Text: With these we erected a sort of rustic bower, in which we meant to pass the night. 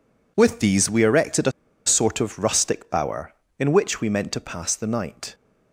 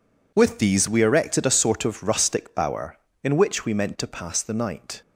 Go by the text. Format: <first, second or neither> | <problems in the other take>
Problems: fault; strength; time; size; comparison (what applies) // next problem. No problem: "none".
second | pauses between "a" and "sort"; slight; at 1.5 s; 0.34 s long